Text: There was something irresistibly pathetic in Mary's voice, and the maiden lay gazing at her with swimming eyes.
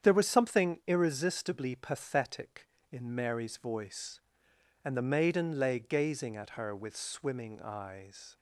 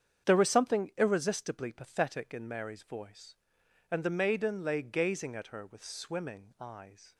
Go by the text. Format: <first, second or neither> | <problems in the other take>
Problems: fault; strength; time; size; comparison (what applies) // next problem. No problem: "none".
neither | starts louder than the rest; strong; the same in both